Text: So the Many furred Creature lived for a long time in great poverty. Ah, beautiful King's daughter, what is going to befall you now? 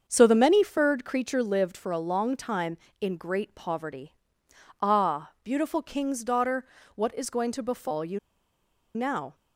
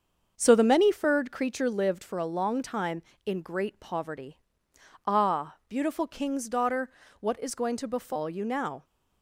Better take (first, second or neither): second